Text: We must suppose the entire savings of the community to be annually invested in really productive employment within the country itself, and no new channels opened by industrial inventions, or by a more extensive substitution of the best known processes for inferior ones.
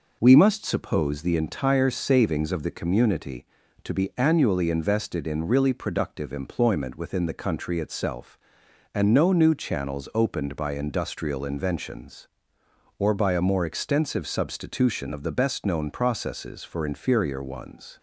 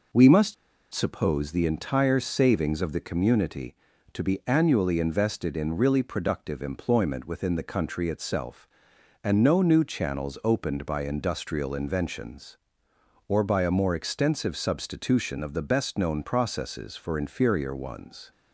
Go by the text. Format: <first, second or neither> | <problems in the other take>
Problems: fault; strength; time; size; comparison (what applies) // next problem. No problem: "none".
first | pauses between "must" and "suppose"; at 0.5 s; 0.39 s long